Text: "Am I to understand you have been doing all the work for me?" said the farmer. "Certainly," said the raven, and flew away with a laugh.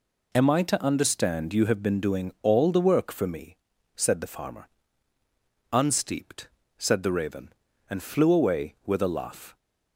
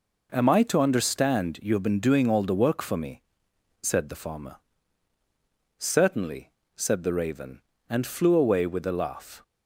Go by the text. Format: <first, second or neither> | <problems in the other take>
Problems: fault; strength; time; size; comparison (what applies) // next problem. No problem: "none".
second | says "Unsteeped" for "Certainly"; at 5.7 s